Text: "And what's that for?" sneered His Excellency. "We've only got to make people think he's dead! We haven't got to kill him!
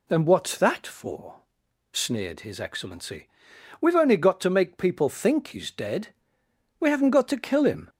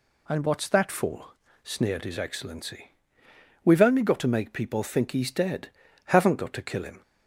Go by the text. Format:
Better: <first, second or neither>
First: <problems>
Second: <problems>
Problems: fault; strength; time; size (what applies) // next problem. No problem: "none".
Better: first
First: none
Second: skips "We"; at 5.8 s